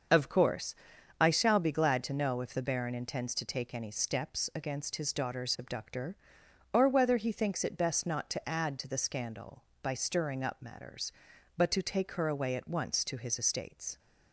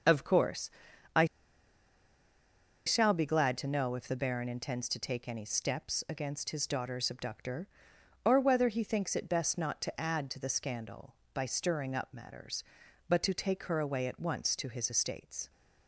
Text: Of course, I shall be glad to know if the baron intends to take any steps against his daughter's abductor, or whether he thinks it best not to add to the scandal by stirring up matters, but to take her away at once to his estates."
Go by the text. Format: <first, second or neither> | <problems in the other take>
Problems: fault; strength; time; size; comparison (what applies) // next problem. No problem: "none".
first | starts louder than the rest; until 3.1 s; 7 dB; also in the first // pauses between "I" and "shall"; strong; at 1.2 s; 1.6 s long